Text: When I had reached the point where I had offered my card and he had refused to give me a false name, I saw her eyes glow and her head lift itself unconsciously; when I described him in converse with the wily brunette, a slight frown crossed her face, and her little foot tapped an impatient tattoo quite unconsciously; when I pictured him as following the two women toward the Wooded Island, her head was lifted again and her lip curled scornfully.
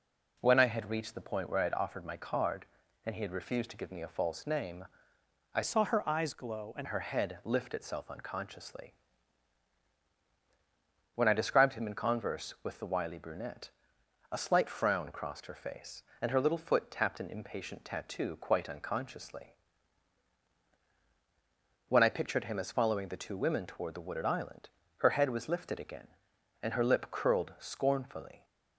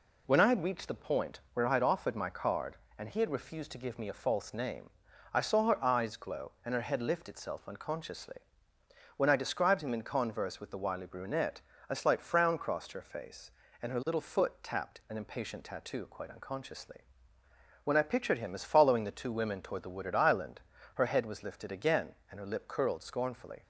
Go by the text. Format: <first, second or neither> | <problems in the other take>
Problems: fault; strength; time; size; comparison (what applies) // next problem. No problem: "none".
second | changes voice from "saw" to "and"; from 5.6 to 6.8 s; 1.2 s long